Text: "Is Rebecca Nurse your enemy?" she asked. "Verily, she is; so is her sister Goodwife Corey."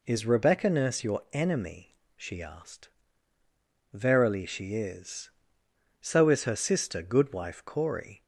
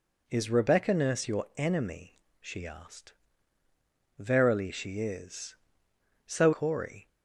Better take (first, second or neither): first